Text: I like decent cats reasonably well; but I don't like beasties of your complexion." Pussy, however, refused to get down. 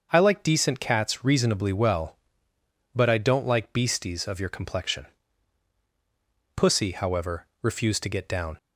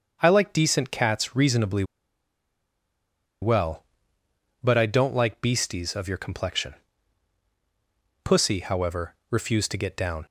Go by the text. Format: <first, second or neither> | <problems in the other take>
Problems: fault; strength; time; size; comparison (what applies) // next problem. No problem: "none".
first | starts louder than the rest; until 1.2 s; 6.5 dB; also in the first // pauses between "reasonably" and "well"; strong; at 1.8 s; 1.5 s long